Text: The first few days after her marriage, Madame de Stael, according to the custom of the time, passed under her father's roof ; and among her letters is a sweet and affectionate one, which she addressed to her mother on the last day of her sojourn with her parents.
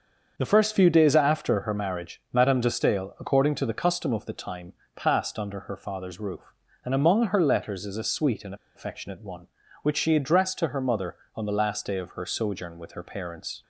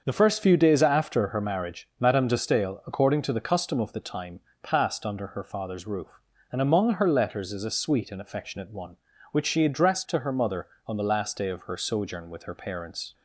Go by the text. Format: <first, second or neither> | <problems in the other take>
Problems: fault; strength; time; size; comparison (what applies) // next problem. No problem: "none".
second | starts louder than the rest; until 1.3 s; 6.5 dB; also in the second // pauses between "and" and "affectionate"; slight; at 8.5 s; 0.20 s long